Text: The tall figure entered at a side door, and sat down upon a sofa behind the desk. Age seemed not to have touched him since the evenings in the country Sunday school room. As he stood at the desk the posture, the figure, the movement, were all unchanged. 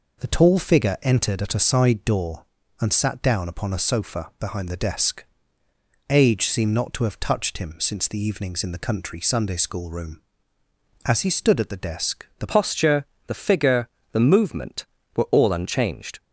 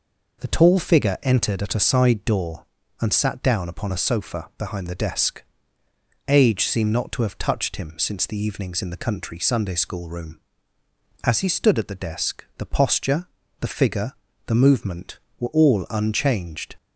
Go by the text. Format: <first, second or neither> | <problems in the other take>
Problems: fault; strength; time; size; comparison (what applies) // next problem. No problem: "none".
second | changes voice at "posture"; from 12.4 s on; 3.7 s long